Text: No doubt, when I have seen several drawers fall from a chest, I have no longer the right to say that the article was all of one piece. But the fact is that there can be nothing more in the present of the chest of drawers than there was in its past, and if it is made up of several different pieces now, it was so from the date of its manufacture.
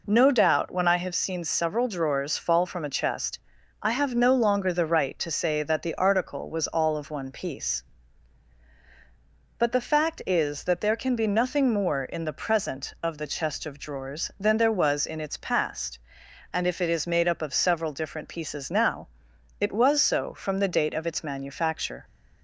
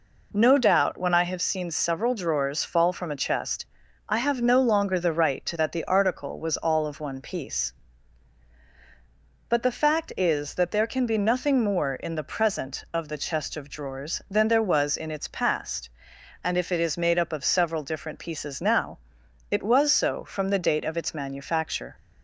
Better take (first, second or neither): first